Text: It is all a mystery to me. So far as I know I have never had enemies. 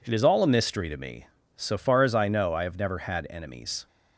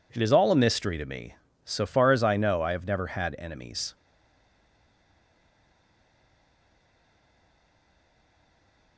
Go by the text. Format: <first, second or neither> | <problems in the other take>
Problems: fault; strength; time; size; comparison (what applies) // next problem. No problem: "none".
first | stays silent after the last word; strong; from 3.9 s on; 5.0 s long